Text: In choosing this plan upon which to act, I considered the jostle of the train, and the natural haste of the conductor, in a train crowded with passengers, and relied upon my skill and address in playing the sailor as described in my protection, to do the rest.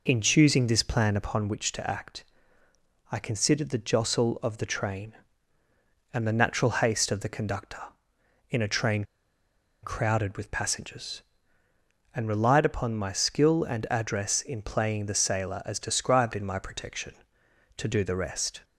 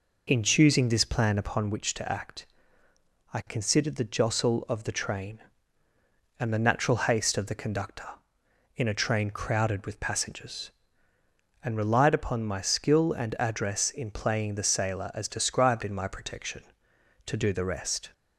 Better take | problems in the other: second | pauses between "train" and "crowded"; noticeable; at 9.0 s; 0.80 s long

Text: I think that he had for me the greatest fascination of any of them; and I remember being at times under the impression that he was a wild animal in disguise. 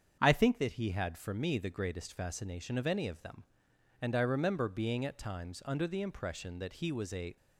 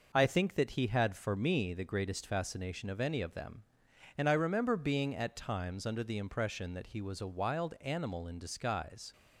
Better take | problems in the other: second | starts louder than the rest; strong; until 1.2 s; 7.5 dB // stops before "wild animal in disguise"; at 7.3 s

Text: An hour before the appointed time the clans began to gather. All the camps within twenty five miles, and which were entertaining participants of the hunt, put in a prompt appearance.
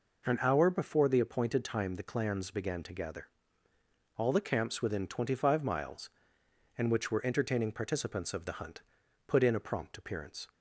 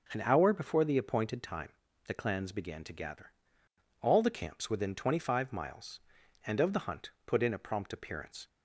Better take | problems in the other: first | starts louder than the rest; until 1.1 s; 6 dB // pauses between "time" and "the"; slight; at 1.6 s; 0.36 s long // skips "which were entertaining participants"; at 6.6 s

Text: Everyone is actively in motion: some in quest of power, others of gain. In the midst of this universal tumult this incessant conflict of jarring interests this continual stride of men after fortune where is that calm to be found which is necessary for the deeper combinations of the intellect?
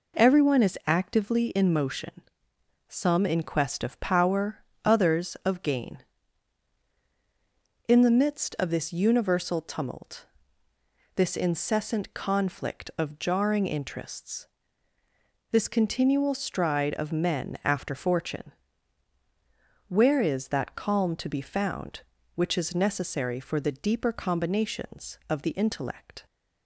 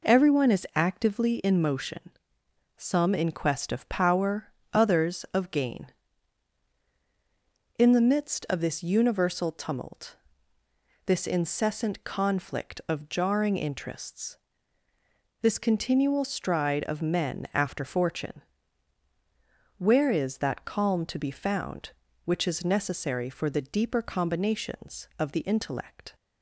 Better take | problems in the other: neither | pauses between "tumult" and "this"; noticeable; the same in both // pauses between "interests" and "this"; the same in both // pauses between "fortune" and "where"; strong; the same in both

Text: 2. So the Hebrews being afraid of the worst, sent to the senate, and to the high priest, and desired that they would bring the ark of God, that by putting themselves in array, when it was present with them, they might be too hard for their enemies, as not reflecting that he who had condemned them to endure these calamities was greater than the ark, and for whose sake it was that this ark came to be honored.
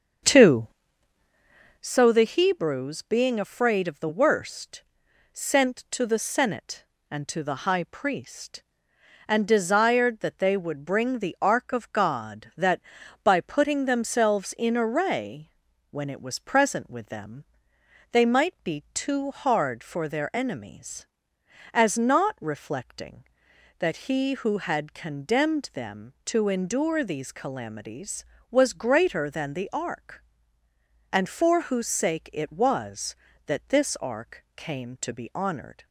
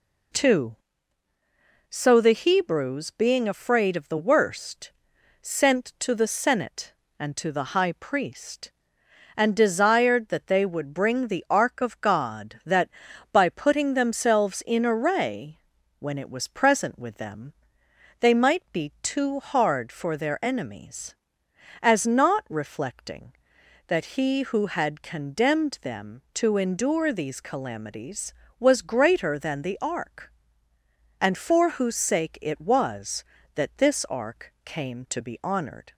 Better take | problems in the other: second | starts louder than the rest; until 1.9 s; 7 dB

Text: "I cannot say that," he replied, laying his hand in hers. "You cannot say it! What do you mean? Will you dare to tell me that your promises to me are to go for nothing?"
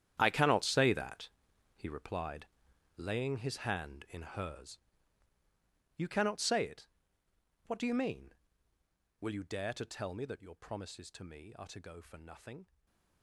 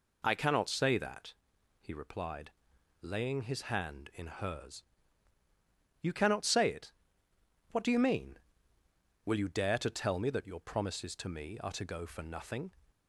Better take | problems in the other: second | gets quieter; strong; throughout; 14 dB // stays silent after the last word; slight; from 12.6 s on; 0.6 s long

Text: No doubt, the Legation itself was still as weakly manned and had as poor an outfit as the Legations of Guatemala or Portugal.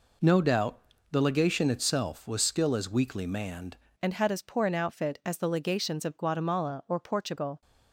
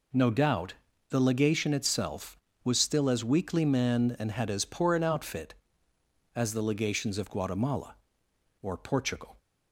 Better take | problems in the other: second | changes voice at "and"; from 3.9 s on; 3.7 s long

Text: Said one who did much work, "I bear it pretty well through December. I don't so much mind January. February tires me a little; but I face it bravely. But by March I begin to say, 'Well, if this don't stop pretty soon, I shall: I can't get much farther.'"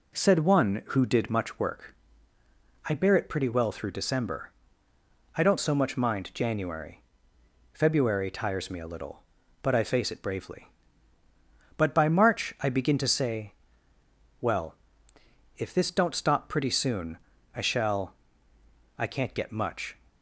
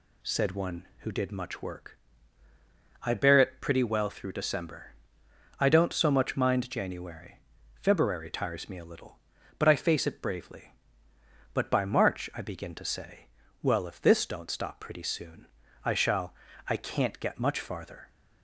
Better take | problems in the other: second | stops before "farther"; at 20.0 s

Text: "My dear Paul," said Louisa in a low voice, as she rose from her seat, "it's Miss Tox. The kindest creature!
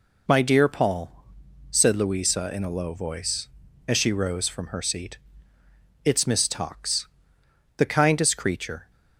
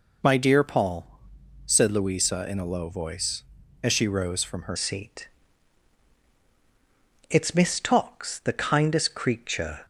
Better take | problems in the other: first | changes voice at "seat"; from 4.7 s on; 5.1 s long

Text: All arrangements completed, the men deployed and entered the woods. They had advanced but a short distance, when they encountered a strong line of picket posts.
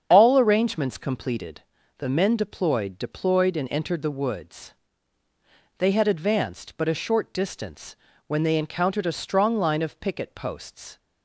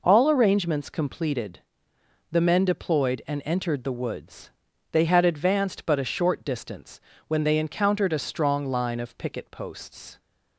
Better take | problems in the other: second | starts louder than the rest; strong; until 1.1 s; 8 dB // says "deployed" twice; at 2.9 s

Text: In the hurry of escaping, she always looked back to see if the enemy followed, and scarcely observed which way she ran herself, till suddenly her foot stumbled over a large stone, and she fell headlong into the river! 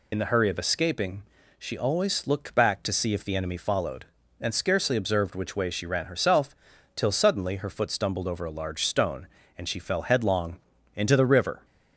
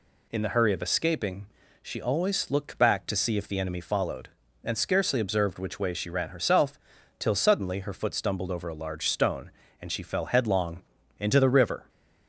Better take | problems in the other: second | loses the start of "In"; at 0.1 s; 55 ms // pauses between "headlong" and "into"; slight; at 10.5 s; 0.36 s long; slight in the second

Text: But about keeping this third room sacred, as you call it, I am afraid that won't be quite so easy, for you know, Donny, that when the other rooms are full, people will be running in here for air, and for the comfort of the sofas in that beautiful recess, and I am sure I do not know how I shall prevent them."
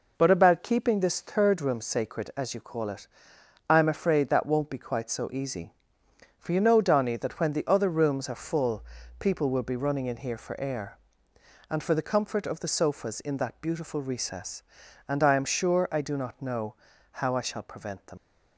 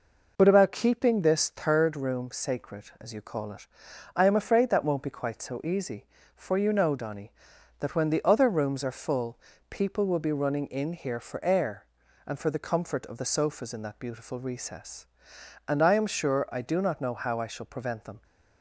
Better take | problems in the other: second | pauses between "know" and "how"; at 16.7 s; 0.44 s long // leaves "them" unfinished; at 18.1 s; 85 ms

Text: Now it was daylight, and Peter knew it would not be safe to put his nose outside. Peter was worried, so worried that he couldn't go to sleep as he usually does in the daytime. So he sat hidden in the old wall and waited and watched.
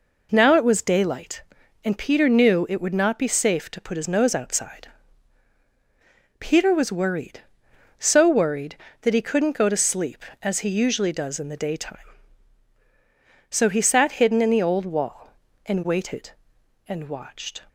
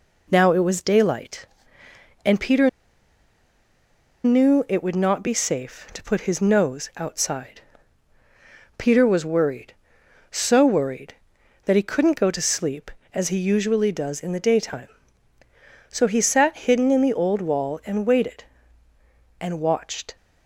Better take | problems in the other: first | pauses between "Peter" and "knew"; strong; at 2.6 s; 1.5 s long

